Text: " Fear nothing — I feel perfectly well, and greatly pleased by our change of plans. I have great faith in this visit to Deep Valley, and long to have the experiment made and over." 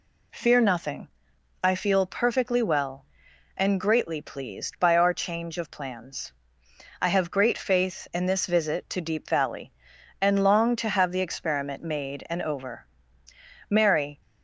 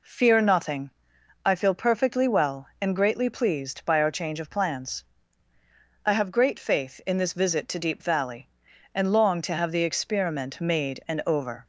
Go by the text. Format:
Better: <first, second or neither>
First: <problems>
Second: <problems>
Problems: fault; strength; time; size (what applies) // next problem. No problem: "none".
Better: second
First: goes on to say "Mary"; from 13.6 s on; 0.52 s long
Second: none